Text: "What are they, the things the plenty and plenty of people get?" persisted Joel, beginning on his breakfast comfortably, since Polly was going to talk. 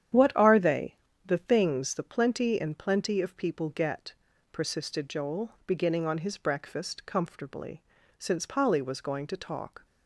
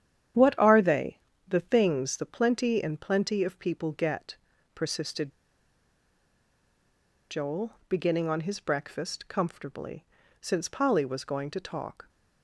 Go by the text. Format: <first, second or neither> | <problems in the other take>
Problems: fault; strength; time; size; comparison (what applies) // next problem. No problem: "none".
first | starts louder than the rest; strong; until 1.7 s; 9.5 dB; strong in the first // pauses between "persisted" and "Joel"; strong; at 5.3 s; 1.9 s long